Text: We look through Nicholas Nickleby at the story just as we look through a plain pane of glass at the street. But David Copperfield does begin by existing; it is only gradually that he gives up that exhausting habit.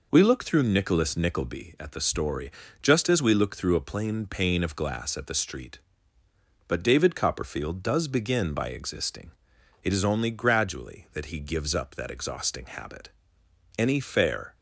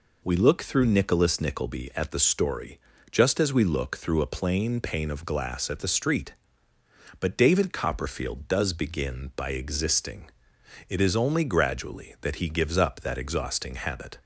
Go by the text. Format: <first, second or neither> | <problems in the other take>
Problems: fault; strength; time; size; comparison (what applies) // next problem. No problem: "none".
second | pauses between "story" and "just"; slight; at 2.4 s; 0.32 s long; slight in the second // goes on to say "Any fair"; noticeable; from 13.7 s on; 0.78 s long